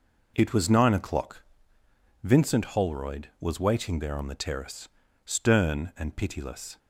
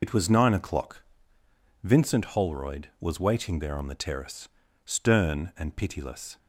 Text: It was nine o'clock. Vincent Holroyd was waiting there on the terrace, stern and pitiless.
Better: first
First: none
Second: loses the start of "It"; at 0.0 s; 65 ms

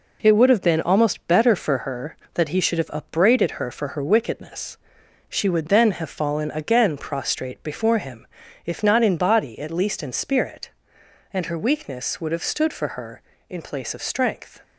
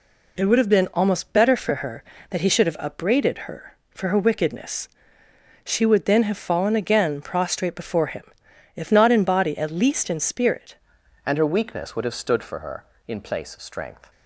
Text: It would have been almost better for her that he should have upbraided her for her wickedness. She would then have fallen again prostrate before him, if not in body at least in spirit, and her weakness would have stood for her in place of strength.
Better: first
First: none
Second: changes voice at "and"; from 11.2 s on; 2.9 s long

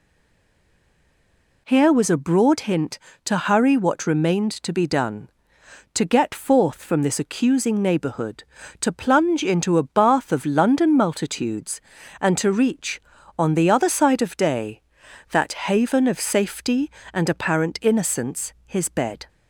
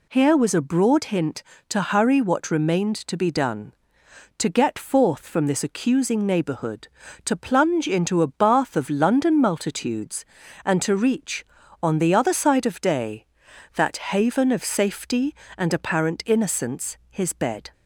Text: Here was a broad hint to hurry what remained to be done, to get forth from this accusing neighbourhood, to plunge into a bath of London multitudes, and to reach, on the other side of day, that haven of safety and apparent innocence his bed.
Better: second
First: stays silent before the first word; noticeable; until 1.6 s; 1.6 s long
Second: none

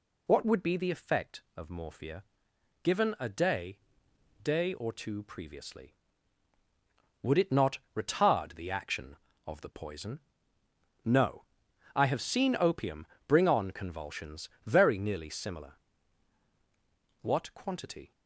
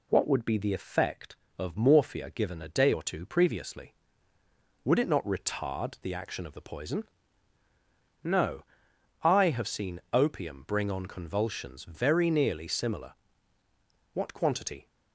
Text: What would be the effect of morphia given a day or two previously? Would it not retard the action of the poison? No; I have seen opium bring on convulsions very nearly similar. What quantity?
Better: second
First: pauses between "morphia" and "given"; noticeable; at 2.2 s; 0.62 s long // says "day" twice; at 4.4 s // pauses between "not" and "retard"; slight; at 7.7 s; 0.18 s long // pauses between "opium" and "bring"; slight; at 13.0 s; 0.18 s long // pauses between "convulsions" and "very"; slight; at 14.4 s; 0.18 s long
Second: none

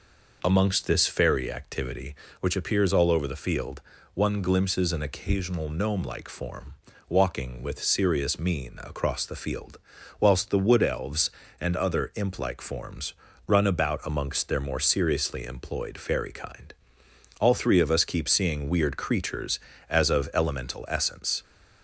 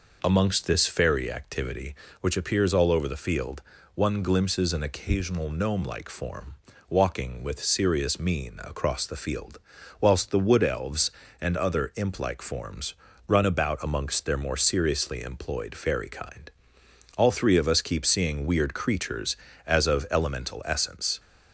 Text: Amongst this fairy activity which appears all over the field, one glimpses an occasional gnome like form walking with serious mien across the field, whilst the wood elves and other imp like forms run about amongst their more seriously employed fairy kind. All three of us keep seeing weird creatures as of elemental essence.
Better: neither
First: pauses between "form" and "walking"; slight; at 6.7 s; 0.36 s long // pauses between "forms" and "run"; slight; at 13.1 s; 0.34 s long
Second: pauses between "form" and "walking"; slight; at 6.5 s; 0.36 s long // pauses between "forms" and "run"; slight; at 12.9 s; 0.34 s long

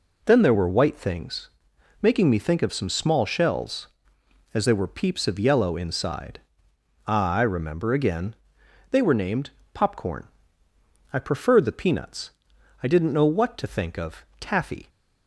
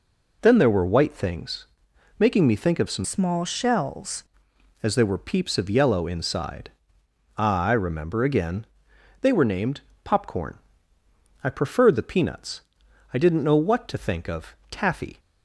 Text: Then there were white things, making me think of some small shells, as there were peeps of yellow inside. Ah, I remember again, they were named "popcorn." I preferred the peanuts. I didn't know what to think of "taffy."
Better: first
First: pauses between "named" and "popcorn"; slight; at 9.5 s; 0.24 s long // pauses between "of" and "taffy"; slight; at 14.2 s; 0.16 s long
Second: changes voice from "small" to "shells"; from 3.0 to 4.2 s; 1.2 s long // pauses between "named" and "popcorn"; slight; at 9.8 s; 0.24 s long // pauses between "of" and "taffy"; slight; at 14.5 s; 0.16 s long

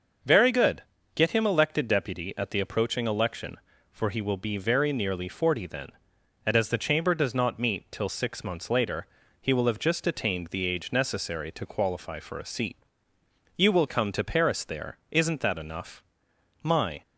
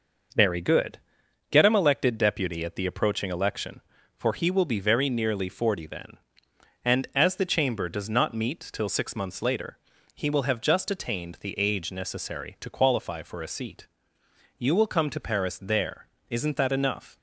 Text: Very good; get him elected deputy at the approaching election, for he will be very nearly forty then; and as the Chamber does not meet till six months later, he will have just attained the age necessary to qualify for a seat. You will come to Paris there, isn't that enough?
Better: second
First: starts louder than the rest; noticeable; until 1.5 s; 6 dB // goes on to say "My"; slight; from 16.6 s on; 0.40 s long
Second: none

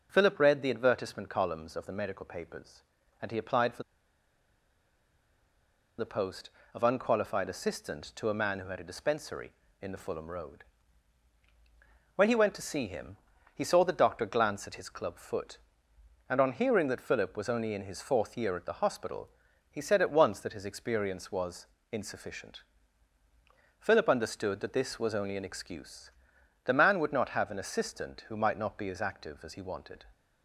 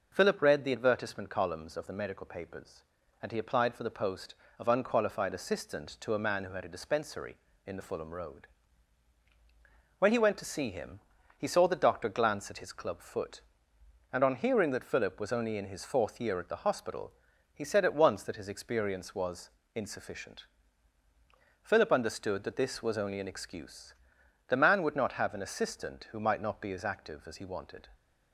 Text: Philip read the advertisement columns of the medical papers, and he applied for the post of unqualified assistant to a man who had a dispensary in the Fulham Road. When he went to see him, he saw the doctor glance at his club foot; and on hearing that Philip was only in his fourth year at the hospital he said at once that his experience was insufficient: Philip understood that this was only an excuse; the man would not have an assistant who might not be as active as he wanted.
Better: second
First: pauses between "for" and "the"; strong; at 3.8 s; 2.1 s long // pauses between "hospital" and "he"; at 19.2 s; 0.42 s long // pauses between "was" and "insufficient"; slight; at 21.6 s; 0.26 s long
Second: pauses between "hospital" and "he"; at 17.1 s; 0.42 s long // pauses between "was" and "insufficient"; slight; at 19.4 s; 0.26 s long

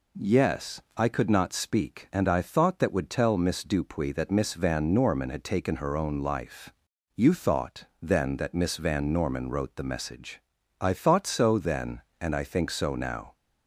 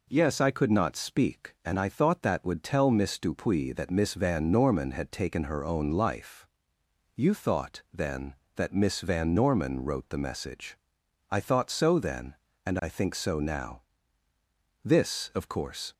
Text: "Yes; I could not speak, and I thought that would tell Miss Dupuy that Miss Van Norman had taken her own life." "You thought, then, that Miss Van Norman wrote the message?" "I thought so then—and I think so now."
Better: first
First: none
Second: goes on to say "This of course"; noticeable; from 14.8 s on; 1.1 s long

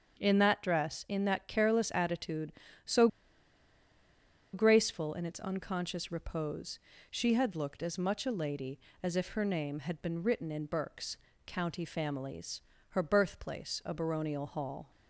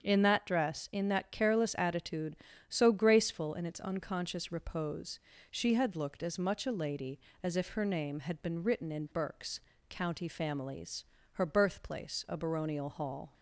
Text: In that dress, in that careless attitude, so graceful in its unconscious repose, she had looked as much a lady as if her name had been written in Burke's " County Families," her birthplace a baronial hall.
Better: second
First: starts louder than the rest; strong; until 1.2 s; 7 dB // pauses between "so" and "graceful"; strong; at 3.0 s; 1.4 s long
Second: starts louder than the rest; until 1.0 s; 7 dB

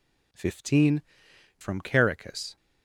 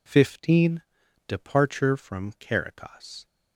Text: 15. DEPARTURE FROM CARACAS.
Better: second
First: skips "DEPARTURE"; at 1.3 s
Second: none

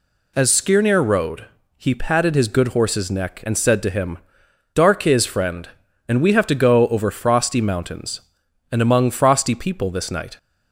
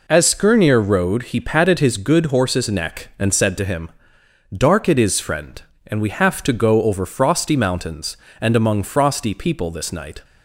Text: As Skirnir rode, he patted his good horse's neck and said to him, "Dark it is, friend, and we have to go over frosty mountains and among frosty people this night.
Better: second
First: skips "it"; at 5.0 s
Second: none

